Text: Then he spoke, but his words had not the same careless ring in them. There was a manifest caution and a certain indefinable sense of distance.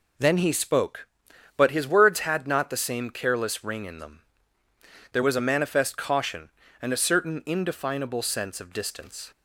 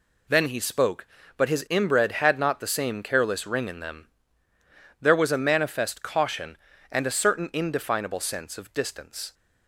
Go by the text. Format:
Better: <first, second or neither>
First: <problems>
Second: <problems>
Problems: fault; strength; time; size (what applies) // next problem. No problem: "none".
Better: first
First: none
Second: says "inbred" for "words"; at 1.7 s